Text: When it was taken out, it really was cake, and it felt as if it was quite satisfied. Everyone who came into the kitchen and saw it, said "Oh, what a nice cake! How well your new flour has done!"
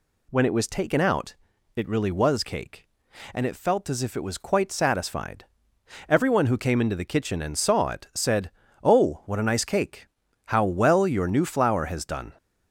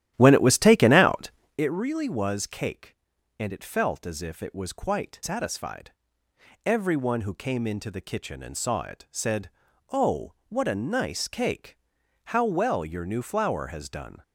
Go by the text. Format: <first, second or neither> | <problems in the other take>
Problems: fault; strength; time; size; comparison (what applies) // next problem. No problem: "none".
first | starts louder than the rest; strong; until 1.6 s; 12.5 dB // pauses between "said" and "Oh"; at 9.4 s; 0.40 s long; slight in the first